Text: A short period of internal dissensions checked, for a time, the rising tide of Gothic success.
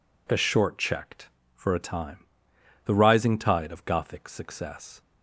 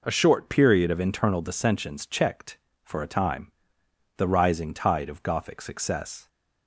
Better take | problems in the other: second | skips "period of internal dissensions"; at 0.7 s

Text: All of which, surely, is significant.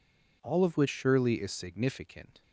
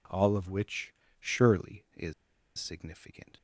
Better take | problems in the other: first | pauses between "is" and "significant"; at 2.1 s; 0.44 s long

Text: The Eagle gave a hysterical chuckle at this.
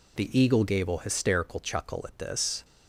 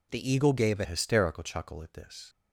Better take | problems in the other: first | changes voice at "hysterical"; from 0.8 s on; 1.4 s long

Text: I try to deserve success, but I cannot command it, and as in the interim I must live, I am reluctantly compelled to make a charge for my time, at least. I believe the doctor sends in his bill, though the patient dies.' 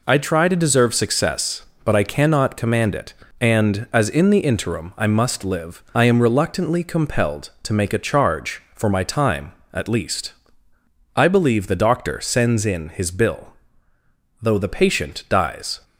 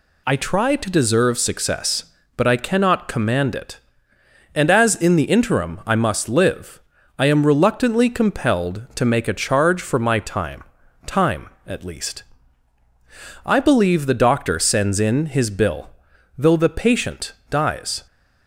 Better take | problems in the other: first | says "time" twice; at 11.0 s // pauses between "patient" and "dies"; slight; at 17.3 s; 0.18 s long

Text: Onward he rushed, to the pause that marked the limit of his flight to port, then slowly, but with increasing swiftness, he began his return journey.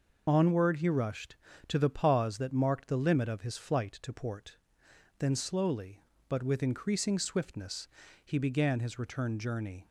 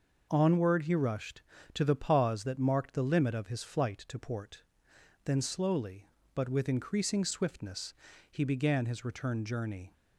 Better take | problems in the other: second | loses the start of "Onward"; at 0.2 s; 30 ms

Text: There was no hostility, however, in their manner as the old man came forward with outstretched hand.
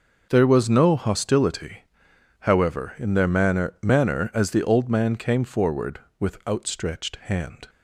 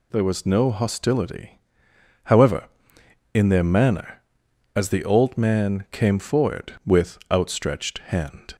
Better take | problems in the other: second | says "manner" twice; at 3.8 s

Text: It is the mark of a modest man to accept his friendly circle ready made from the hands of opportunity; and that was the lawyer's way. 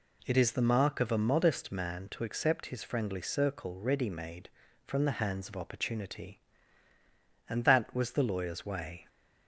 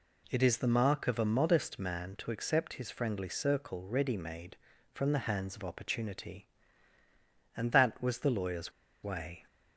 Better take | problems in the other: first | pauses between "lawyer's" and "way"; slight; at 8.7 s; 0.30 s long

